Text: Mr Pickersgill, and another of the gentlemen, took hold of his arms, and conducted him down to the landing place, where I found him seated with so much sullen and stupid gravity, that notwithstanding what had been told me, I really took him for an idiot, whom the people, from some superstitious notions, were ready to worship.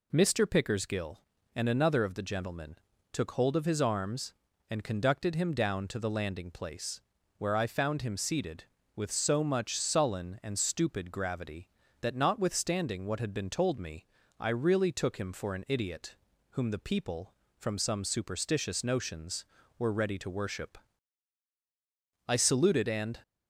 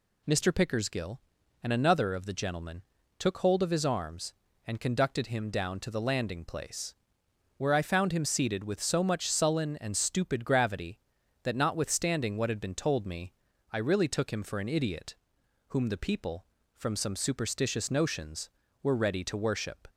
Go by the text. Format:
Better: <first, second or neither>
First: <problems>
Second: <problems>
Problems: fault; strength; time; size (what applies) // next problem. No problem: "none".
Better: second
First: goes on to say "I saluted and"; noticeable; from 22.2 s on; 0.92 s long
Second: none